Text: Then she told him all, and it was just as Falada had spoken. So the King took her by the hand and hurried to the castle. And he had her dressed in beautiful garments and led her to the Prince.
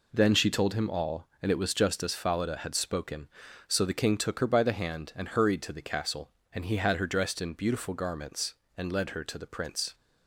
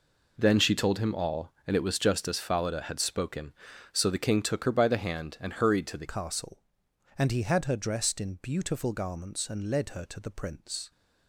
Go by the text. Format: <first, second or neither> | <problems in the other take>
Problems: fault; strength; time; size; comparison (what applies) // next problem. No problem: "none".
first | changes voice at "castle"; from 6.0 s on; 4.9 s long